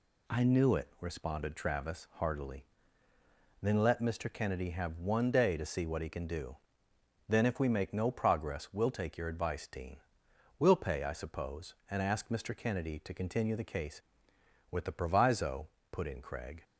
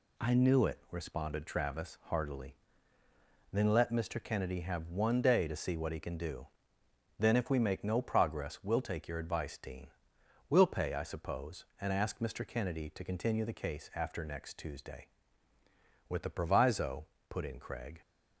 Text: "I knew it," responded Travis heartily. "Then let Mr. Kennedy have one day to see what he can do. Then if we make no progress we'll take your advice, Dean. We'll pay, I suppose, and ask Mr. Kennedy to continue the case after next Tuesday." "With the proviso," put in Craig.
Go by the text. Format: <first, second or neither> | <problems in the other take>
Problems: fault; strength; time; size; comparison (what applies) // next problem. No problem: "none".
second | skips "after next Tuesday"; at 14.3 s